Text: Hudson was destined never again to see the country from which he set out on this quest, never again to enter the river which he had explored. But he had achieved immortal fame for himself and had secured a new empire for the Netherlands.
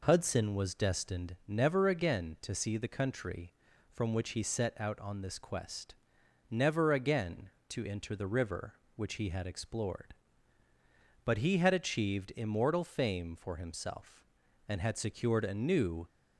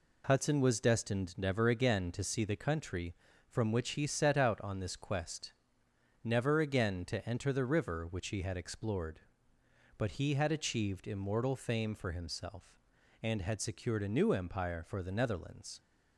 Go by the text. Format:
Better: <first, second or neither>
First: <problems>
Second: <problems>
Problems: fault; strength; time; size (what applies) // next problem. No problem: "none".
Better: second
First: stops before "empire for the Netherlands"; at 16.0 s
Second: none